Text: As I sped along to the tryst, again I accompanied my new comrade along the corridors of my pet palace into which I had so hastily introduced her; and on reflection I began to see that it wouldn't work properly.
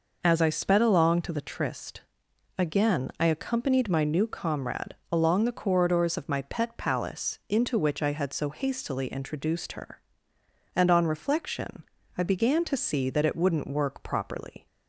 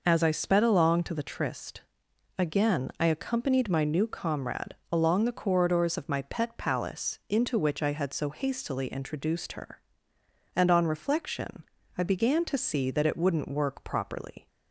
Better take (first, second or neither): neither